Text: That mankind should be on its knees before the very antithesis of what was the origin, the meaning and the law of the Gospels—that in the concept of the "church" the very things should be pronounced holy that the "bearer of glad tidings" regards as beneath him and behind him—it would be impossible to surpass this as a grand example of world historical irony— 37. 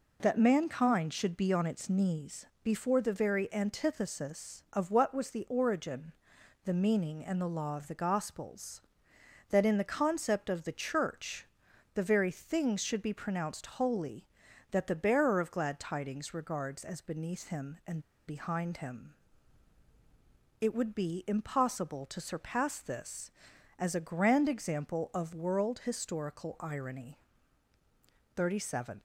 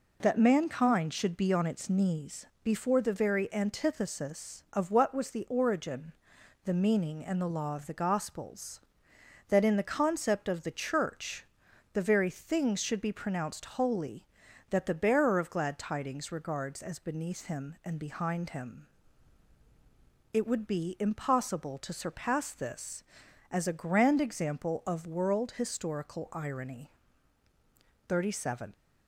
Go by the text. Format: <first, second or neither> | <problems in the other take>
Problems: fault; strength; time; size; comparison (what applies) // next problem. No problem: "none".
second | pauses between "knees" and "before"; slight; at 2.4 s; 0.18 s long; slight in the second // pauses between "church" and "the"; noticeable; at 11.4 s; 0.48 s long; noticeable in the second // pauses between "and" and "behind"; slight; at 17.9 s; 0.28 s long